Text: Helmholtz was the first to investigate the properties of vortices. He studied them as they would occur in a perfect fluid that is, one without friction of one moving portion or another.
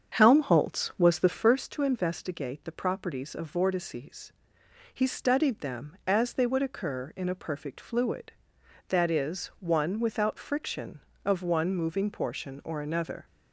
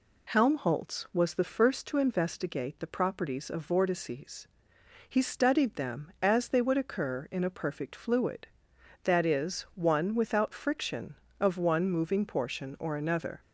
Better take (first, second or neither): second